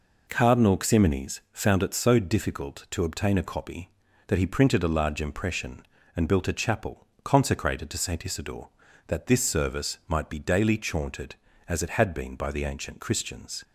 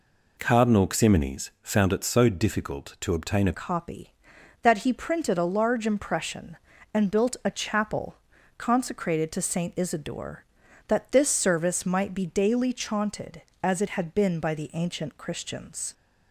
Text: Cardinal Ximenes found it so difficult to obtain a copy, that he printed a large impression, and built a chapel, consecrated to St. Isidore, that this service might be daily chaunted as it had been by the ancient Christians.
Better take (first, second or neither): first